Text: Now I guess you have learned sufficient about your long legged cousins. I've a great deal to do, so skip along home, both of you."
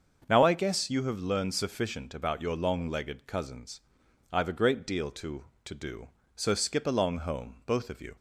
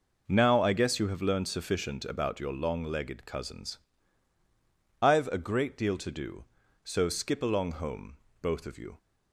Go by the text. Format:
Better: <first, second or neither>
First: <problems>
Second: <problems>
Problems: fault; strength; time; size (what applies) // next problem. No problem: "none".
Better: second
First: starts louder than the rest; until 1.2 s; 6.5 dB // says "to" twice; at 5.6 s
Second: none